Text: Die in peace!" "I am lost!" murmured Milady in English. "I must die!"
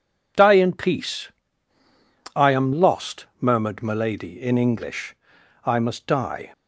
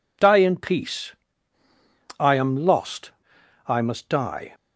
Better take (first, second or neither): first